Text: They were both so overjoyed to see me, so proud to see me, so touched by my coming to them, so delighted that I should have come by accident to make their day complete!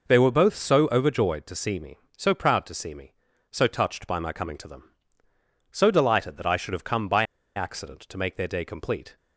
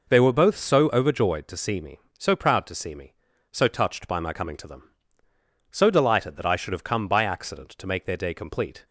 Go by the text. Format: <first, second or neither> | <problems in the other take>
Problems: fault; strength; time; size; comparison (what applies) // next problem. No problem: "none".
second | pauses between "by" and "accident"; slight; at 7.2 s; 0.32 s long